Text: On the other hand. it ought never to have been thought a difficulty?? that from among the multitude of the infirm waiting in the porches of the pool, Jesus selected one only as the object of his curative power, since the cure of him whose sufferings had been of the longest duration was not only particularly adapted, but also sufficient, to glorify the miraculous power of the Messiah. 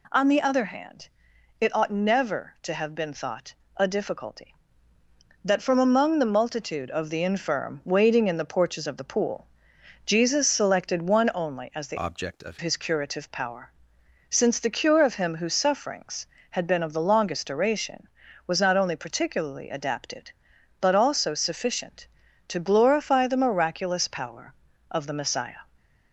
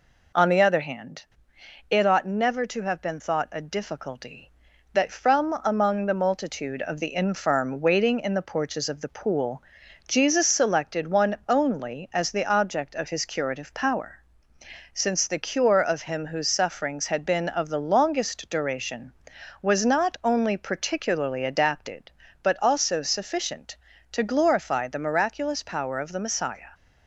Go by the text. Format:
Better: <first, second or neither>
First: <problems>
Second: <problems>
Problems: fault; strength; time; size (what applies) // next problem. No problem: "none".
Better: second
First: pauses between "thought" and "a"; slight; at 3.5 s; 0.22 s long // changes voice from "object" to "of"; from 11.9 to 12.5 s; 0.6 s long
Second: none